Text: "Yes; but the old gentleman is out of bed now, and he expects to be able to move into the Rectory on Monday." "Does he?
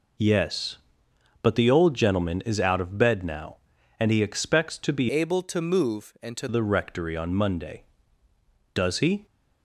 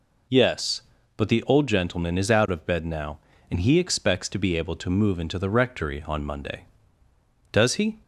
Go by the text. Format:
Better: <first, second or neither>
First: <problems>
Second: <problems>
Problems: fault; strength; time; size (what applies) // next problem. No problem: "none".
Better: second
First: changes voice from "able" to "into"; from 5.0 to 6.4 s; 1.4 s long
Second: none